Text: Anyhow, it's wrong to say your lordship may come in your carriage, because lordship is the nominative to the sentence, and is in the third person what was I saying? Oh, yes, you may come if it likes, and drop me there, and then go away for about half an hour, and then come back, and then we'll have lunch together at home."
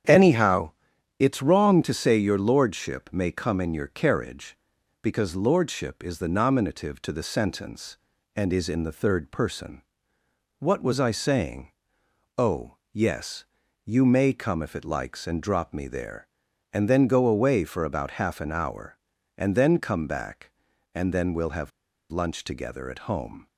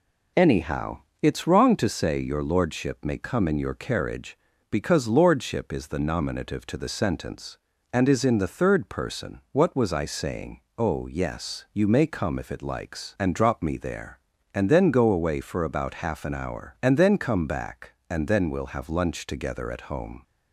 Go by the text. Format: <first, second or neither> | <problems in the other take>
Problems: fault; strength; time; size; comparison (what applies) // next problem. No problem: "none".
second | starts louder than the rest; strong; until 1.5 s; 9 dB // pauses between "person" and "what"; noticeable; at 9.8 s; 0.78 s long // pauses between "have" and "lunch"; at 21.7 s; 0.42 s long